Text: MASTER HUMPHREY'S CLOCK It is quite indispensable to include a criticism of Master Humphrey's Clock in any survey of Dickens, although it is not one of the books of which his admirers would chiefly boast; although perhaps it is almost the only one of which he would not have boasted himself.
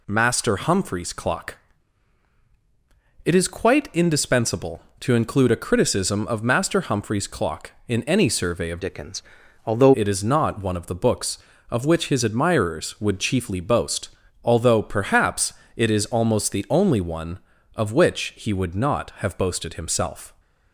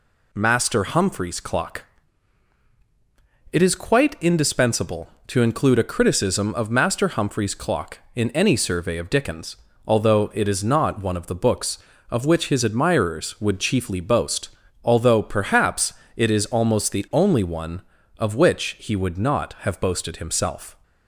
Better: second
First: pauses between "CLOCK" and "It"; strong; at 1.5 s; 1.6 s long // changes voice from "Dickens" to "although"; from 8.8 to 9.9 s; 1.1 s long // pauses between "perhaps" and "it"; slight; at 15.5 s; 0.24 s long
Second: pauses between "CLOCK" and "It"; strong; at 1.8 s; 1.6 s long // pauses between "perhaps" and "it"; slight; at 15.9 s; 0.24 s long

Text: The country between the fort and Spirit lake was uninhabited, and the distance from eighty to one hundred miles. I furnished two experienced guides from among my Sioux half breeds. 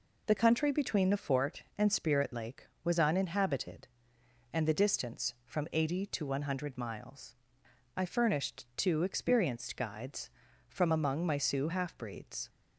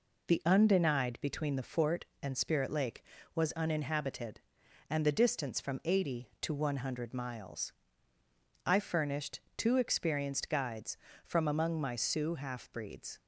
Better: first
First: none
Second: says "undenied" for "country"; at 0.4 s // pauses between "furnished" and "two"; slight; at 9.3 s; 0.18 s long

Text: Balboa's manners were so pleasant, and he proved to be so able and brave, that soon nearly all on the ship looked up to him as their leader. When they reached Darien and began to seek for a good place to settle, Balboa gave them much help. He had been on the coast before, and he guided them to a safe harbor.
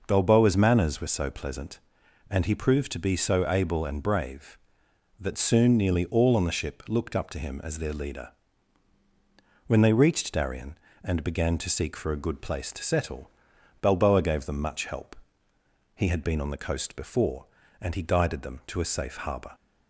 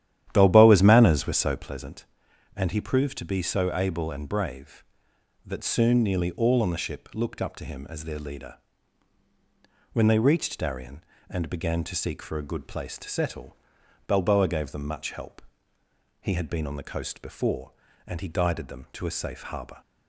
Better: first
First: none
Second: starts louder than the rest; strong; until 1.7 s; 11.5 dB

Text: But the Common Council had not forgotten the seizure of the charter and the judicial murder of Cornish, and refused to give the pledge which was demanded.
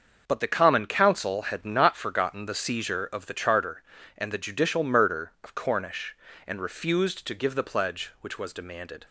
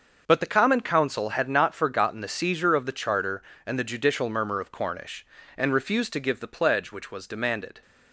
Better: first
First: starts louder than the rest; until 1.2 s; 6.5 dB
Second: starts louder than the rest; until 1.2 s; 6.5 dB // says "murmur" for "murder"; at 4.3 s

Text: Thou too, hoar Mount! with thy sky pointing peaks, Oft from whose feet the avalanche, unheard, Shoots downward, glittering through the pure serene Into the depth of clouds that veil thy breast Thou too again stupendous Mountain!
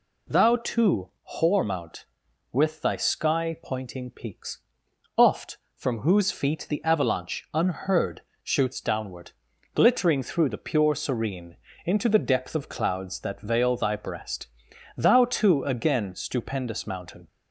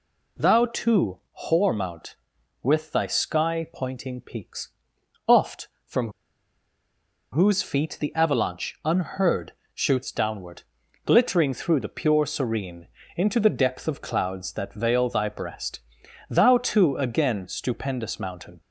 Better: first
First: pauses between "serene" and "Into"; slight; at 11.5 s; 0.30 s long // pauses between "breast" and "Thou"; noticeable; at 14.4 s; 0.50 s long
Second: pauses between "from" and "whose"; at 6.0 s; 1.2 s long // pauses between "serene" and "Into"; slight; at 12.8 s; 0.30 s long // pauses between "breast" and "Thou"; noticeable; at 15.7 s; 0.50 s long

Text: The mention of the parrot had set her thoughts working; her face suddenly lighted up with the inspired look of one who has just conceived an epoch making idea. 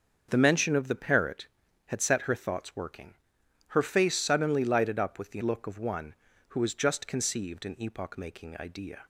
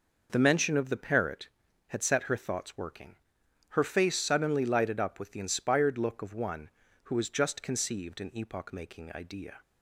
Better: second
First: starts louder than the rest; until 1.3 s; 6.5 dB // skips "inspired"; at 5.4 s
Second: none

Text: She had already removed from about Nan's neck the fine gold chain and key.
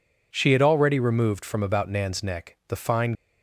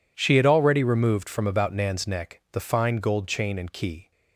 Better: second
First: stops before "gold chain and key"; at 3.1 s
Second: none

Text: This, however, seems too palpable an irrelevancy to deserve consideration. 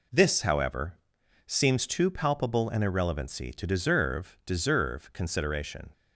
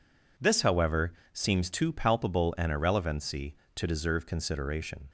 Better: second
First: says "deserve" twice; at 4.4 s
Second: none

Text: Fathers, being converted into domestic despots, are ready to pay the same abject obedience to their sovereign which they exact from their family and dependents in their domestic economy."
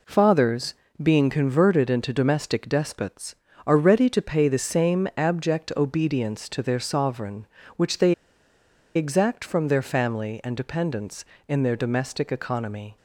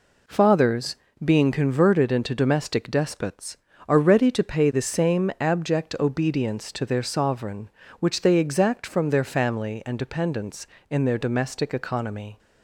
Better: second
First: pauses between "they" and "exact"; noticeable; at 8.1 s; 0.82 s long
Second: none

